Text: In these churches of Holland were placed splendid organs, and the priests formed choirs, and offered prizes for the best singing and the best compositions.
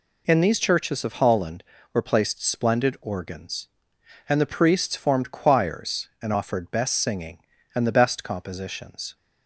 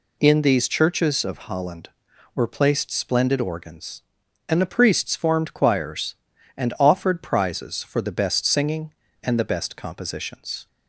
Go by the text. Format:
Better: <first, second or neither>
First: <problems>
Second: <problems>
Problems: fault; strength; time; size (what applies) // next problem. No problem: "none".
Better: second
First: skips "prizes for the"; at 6.7 s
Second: none